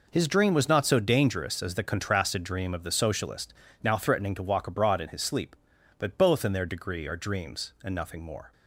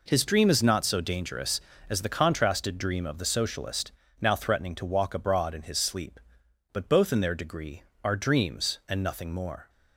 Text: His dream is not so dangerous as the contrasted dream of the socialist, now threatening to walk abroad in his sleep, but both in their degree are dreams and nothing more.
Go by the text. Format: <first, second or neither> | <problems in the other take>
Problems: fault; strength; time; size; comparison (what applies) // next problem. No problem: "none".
second | says "was" for "is"; at 0.5 s